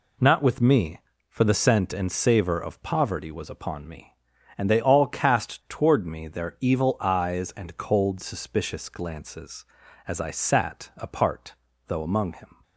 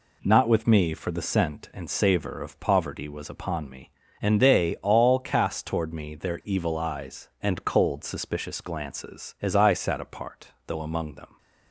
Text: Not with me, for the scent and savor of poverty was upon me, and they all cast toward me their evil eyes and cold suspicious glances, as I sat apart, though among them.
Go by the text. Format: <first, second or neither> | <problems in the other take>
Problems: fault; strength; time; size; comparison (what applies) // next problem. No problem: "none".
second | says "him" for "them"; at 12.3 s